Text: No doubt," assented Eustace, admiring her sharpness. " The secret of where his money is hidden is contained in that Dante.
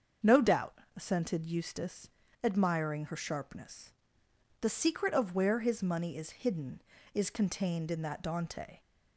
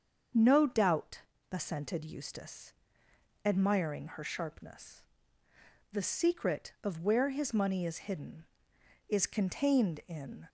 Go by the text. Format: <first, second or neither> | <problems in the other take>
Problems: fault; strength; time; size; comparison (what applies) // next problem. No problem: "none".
first | starts louder than the rest; strong; until 1.6 s; 7 dB; strong in the first // stops before "that Dante"; at 10.4 s